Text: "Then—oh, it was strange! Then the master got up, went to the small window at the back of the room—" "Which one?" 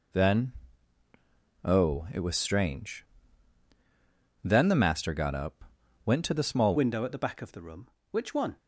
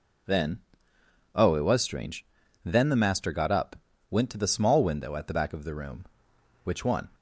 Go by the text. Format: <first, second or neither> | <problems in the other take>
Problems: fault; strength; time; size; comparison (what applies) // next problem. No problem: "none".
second | changes voice at "window"; from 6.7 s on; 1.8 s long